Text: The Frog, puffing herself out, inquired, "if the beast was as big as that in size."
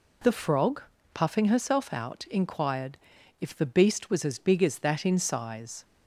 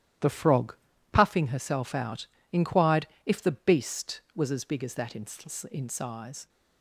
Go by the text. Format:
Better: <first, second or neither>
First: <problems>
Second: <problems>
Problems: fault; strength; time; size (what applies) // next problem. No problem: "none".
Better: first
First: none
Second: says "in" twice; at 5.7 s